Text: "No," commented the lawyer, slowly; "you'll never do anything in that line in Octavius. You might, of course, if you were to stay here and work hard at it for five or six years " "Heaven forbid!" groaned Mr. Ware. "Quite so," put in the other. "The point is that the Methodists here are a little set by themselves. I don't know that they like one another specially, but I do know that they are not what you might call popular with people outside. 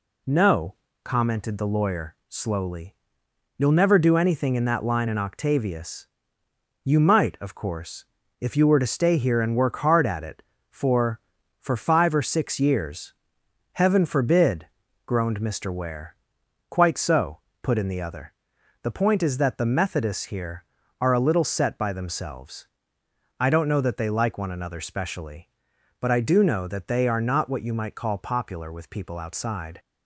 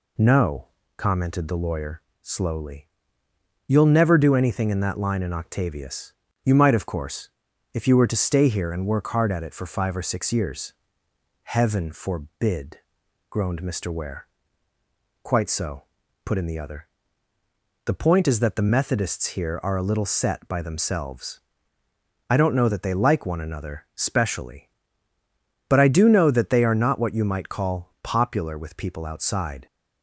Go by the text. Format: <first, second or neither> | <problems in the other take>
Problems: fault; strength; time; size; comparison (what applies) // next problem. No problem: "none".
second | says "for" twice; at 11.5 s